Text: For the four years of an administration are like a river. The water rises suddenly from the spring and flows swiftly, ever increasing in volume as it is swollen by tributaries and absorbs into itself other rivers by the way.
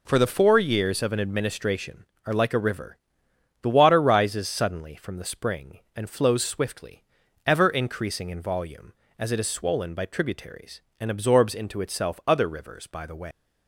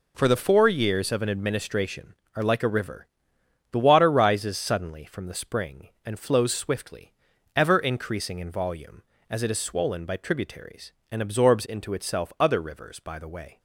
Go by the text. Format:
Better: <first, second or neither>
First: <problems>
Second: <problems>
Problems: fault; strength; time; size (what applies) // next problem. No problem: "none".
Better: second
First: leaves "way" unfinished; at 13.3 s; 155 ms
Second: none